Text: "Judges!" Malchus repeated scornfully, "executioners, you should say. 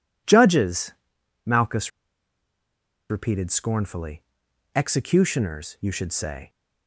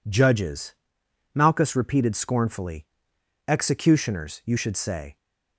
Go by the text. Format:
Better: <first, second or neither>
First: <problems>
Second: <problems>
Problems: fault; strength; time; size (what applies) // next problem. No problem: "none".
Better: second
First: pauses between "Malchus" and "repeated"; at 1.8 s; 1.2 s long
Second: none